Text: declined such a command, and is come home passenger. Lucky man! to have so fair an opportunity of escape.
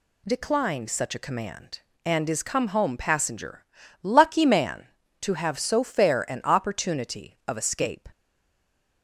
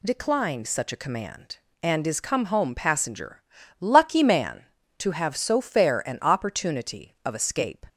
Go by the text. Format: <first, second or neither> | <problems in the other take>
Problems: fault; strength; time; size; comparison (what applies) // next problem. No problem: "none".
second | stays silent after the last word; slight; from 8.1 s on; 0.9 s long